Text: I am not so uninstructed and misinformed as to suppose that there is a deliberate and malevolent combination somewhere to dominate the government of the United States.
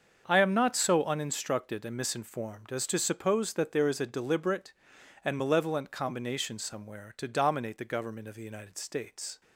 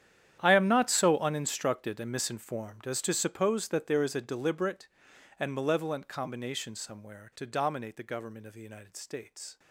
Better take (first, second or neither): first